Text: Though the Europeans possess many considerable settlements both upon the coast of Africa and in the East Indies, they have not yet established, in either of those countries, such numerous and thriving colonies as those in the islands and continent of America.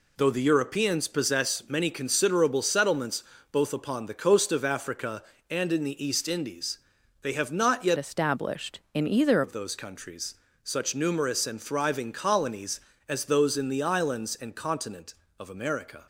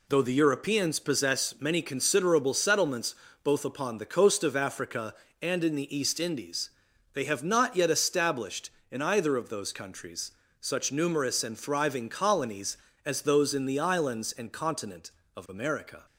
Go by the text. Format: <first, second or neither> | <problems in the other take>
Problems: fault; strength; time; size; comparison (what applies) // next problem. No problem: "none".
second | pauses between "settlements" and "both"; slight; at 3.2 s; 0.28 s long; slight in the second // changes voice from "established" to "either"; from 7.9 to 9.4 s; 1.5 s long